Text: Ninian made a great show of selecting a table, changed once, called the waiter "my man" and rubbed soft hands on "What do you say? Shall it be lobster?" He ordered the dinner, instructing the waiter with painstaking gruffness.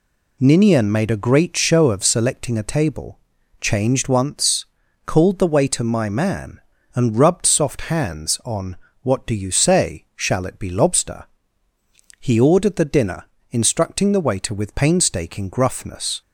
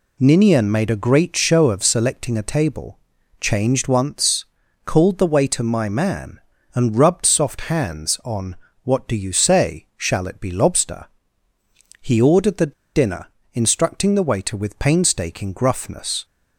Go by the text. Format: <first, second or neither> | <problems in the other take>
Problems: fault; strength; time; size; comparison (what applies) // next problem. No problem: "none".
first | pauses between "on" and "What"; slight; at 8.5 s; 0.28 s long; slight in the first // pauses between "the" and "dinner"; slight; at 12.7 s; 0.23 s long